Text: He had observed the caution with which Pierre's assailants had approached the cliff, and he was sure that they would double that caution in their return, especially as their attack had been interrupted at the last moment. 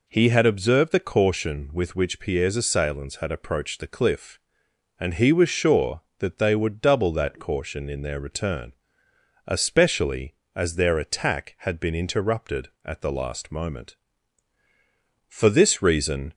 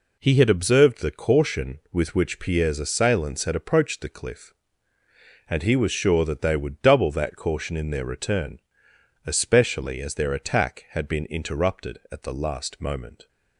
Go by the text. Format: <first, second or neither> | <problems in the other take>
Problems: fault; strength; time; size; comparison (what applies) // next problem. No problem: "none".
second | goes on to say "For this reason"; noticeable; from 15.2 s on; 1.0 s long